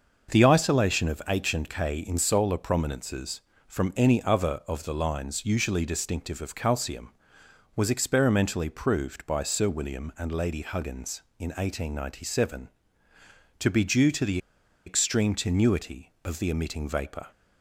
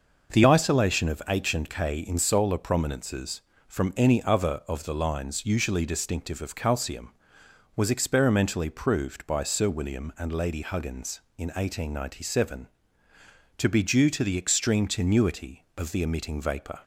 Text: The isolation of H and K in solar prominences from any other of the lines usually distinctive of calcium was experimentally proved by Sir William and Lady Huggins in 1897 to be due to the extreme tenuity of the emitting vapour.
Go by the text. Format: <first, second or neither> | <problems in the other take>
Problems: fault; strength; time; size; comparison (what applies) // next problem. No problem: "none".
second | starts louder than the rest; noticeable; until 1.3 s; 6 dB // pauses between "the" and "extreme"; noticeable; at 14.3 s; 0.48 s long